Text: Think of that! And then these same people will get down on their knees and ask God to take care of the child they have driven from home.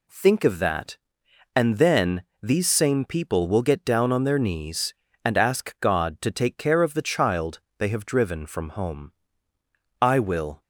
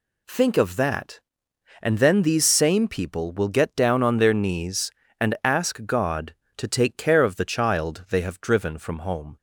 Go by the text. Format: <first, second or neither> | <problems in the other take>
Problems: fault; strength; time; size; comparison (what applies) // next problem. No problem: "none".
second | pauses between "then" and "these"; slight; at 2.2 s; 0.18 s long // pauses between "child" and "they"; slight; at 7.5 s; 0.18 s long // goes on to say "I will"; from 10.0 s on; 0.60 s long